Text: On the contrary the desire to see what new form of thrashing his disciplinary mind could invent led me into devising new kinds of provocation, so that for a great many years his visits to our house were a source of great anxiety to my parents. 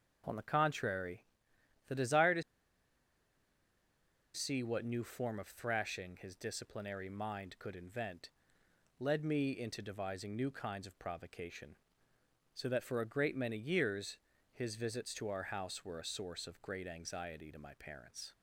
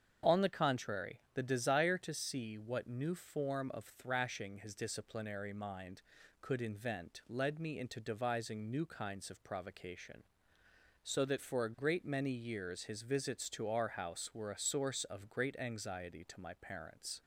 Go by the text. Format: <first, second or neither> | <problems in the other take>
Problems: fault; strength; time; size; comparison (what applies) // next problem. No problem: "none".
second | starts louder than the rest; strong; until 1.8 s; 7 dB; strong in the second // pauses between "contrary" and "the"; noticeable; at 1.2 s; 0.62 s long // pauses between "to" and "see"; strong; at 2.4 s; 1.9 s long // pauses between "invent" and "led"; noticeable; at 8.2 s; 0.68 s long // pauses between "years" and "his"; at 14.1 s; 0.38 s long